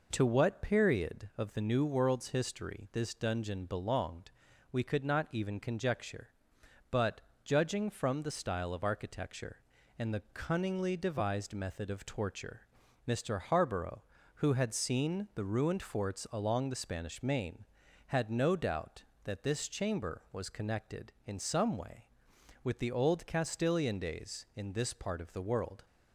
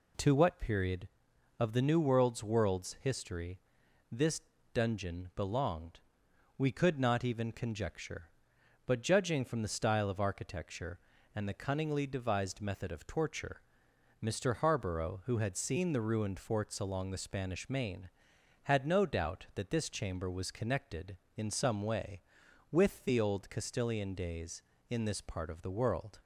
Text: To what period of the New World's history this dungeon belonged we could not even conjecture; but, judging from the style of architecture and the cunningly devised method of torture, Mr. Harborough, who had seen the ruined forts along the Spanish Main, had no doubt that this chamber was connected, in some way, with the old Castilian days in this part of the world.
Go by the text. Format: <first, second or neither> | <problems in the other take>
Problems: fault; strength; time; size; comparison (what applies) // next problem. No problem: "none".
first | says "World's" twice; at 2.4 s // pauses between "history" and "this"; noticeable; at 3.5 s; 0.50 s long // pauses between "this" and "dungeon"; slight; at 4.4 s; 0.30 s long // pauses between "belonged" and "we"; noticeable; at 5.9 s; 0.58 s long; also in the first